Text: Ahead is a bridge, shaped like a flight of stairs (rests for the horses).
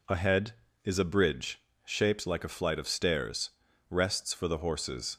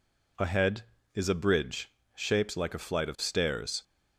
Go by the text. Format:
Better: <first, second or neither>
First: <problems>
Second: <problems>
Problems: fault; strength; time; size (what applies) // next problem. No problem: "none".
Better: first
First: none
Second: stops before "rests for the horses"; at 3.8 s